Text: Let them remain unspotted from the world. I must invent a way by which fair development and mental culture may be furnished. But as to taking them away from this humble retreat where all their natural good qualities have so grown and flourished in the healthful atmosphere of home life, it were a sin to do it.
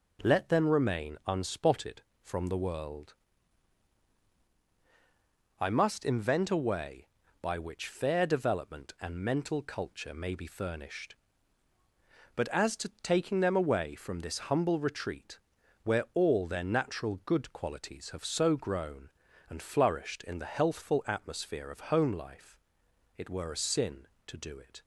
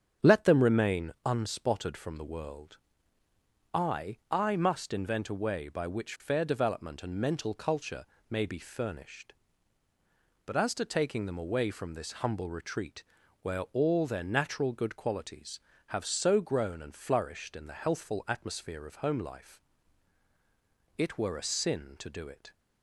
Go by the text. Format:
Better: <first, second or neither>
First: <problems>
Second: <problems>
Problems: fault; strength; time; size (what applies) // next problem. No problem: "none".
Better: first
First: pauses between "retreat" and "where"; noticeable; at 15.3 s; 0.46 s long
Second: starts louder than the rest; strong; until 1.3 s; 8 dB // says "I" twice; at 4.2 s // pauses between "culture" and "may"; slight; at 8.0 s; 0.24 s long // pauses between "retreat" and "where"; at 13.0 s; 0.38 s long